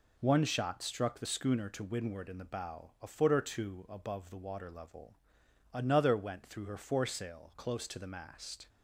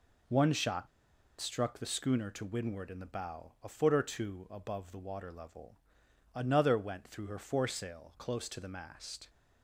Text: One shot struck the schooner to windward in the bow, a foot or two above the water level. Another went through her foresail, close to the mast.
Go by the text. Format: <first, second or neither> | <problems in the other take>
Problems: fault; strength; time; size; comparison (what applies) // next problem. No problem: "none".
first | pauses between "shot" and "struck"; noticeable; at 0.8 s; 0.51 s long